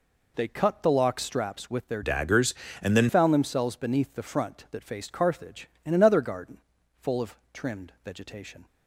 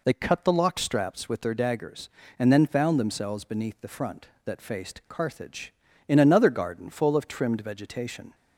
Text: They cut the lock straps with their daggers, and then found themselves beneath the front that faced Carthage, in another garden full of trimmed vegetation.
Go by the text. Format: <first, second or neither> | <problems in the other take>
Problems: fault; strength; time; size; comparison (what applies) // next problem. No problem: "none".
second | changes voice from "daggers" to "then"; from 2.0 to 3.0 s; 1.0 s long // pauses between "garden" and "full"; at 6.5 s; 0.42 s long // pauses between "of" and "trimmed"; slight; at 7.3 s; 0.16 s long